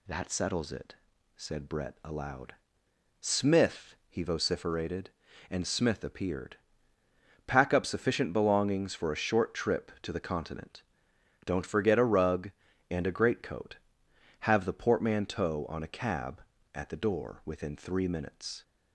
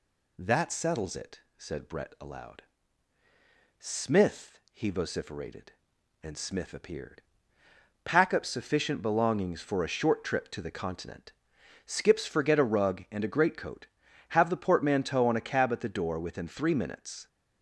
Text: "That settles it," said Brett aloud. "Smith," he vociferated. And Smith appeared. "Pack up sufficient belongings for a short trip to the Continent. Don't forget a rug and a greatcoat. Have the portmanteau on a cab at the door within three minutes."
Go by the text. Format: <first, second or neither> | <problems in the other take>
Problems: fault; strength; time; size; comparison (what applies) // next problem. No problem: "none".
first | says "Skips" for "Don't"; at 11.8 s